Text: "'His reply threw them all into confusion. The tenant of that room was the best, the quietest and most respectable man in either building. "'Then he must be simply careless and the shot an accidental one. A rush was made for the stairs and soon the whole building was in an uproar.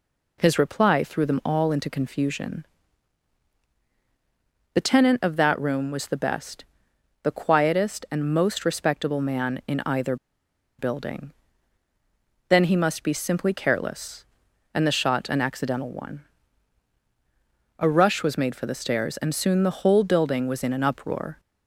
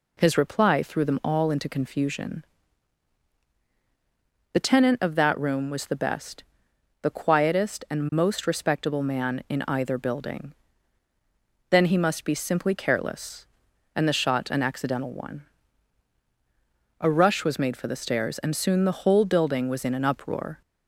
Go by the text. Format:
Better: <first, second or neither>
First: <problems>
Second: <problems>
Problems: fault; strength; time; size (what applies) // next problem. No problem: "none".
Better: second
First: pauses between "either" and "building"; noticeable; at 10.1 s; 0.63 s long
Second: none